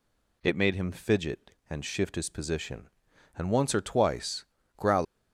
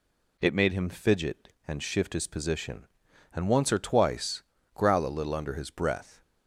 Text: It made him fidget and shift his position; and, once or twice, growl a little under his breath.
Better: second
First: stops before "a little under his breath"; at 5.0 s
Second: none

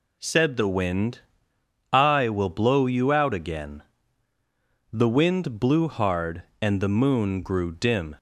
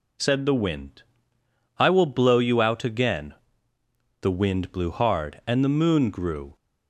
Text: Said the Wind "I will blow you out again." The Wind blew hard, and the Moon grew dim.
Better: first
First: pauses between "Wind" and "I"; noticeable; at 1.2 s; 0.72 s long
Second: pauses between "Wind" and "I"; noticeable; at 1.0 s; 0.74 s long // stops before "dim"; at 6.5 s

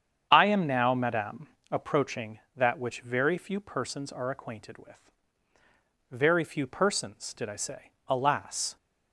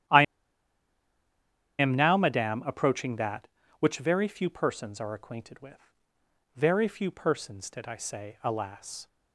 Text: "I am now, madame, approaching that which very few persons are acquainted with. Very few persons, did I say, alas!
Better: first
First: starts louder than the rest; strong; until 1.3 s; 8.5 dB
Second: starts louder than the rest; strong; until 2.6 s; 11.5 dB // pauses between "I" and "am"; strong; at 0.2 s; 1.5 s long

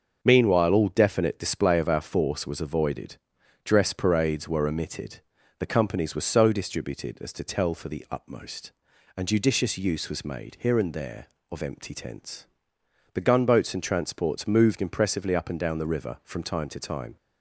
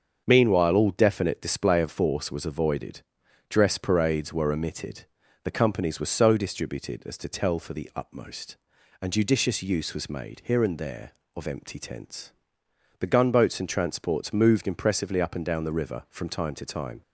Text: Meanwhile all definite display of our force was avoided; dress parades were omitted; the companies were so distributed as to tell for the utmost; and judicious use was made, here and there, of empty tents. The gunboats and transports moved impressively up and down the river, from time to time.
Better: first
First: starts louder than the rest; until 1.2 s; 6.5 dB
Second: starts louder than the rest; until 1.2 s; 7 dB // skips "our"; at 1.8 s

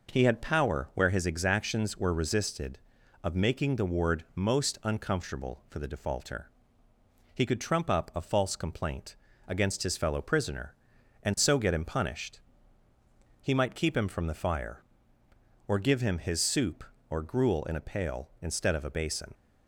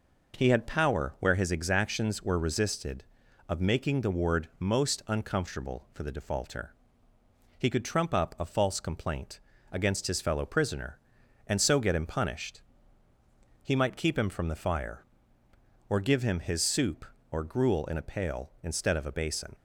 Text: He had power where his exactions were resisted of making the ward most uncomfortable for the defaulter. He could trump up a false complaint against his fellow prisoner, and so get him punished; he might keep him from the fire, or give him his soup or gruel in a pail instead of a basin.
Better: neither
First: pauses between "complaint" and "against"; slight; at 9.1 s; 0.32 s long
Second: pauses between "complaint" and "against"; slight; at 9.3 s; 0.32 s long

